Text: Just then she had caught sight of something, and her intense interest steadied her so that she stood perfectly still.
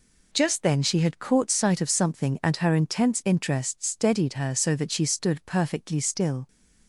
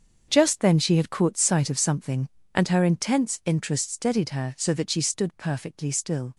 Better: first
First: none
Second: gets quieter; strong; throughout; 12.5 dB

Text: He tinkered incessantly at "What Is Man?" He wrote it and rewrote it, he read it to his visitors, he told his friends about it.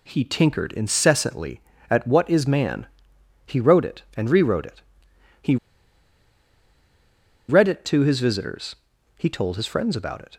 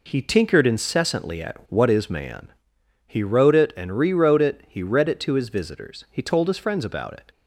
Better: second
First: pauses between "he" and "read"; strong; at 5.5 s; 1.9 s long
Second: none

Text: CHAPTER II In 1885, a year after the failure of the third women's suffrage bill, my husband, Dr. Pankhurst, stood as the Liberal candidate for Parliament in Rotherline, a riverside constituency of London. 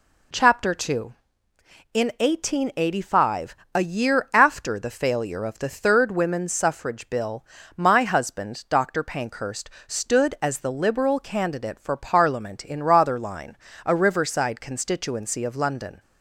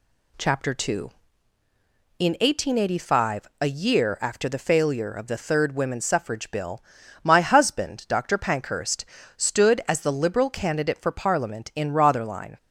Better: first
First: none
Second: stops before "a riverside constituency of London"; at 12.5 s

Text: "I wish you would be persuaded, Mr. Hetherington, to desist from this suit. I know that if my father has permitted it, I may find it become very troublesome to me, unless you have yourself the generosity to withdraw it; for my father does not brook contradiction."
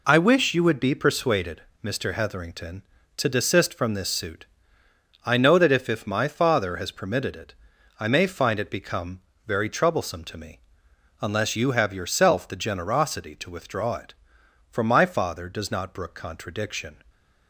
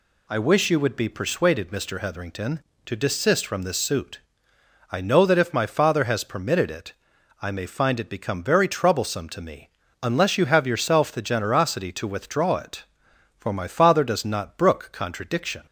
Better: second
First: says "if" twice; at 5.8 s // pauses between "become" and "very"; slight; at 9.2 s; 0.24 s long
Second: none

